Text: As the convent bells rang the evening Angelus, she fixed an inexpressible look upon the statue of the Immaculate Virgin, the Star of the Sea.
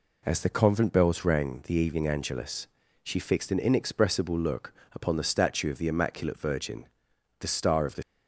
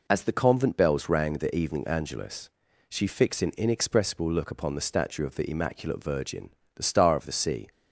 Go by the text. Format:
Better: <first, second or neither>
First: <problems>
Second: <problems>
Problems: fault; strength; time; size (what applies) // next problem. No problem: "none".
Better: second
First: pauses between "look" and "upon"; slight; at 4.7 s; 0.22 s long // stops before "Sea"; at 8.0 s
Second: none